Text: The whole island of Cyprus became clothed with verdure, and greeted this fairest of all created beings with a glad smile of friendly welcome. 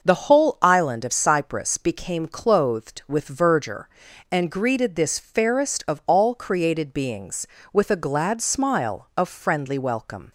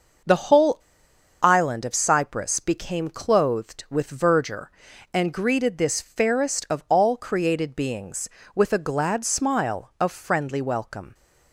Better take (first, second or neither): first